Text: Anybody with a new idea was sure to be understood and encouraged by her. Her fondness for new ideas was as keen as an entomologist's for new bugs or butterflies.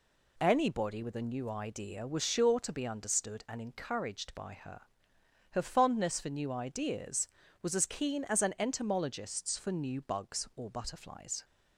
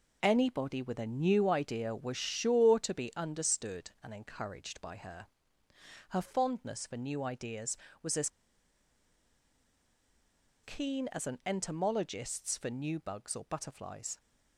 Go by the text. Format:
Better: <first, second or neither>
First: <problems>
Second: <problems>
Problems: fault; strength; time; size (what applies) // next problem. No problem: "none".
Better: first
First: none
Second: pauses between "as" and "keen"; strong; at 8.2 s; 2.3 s long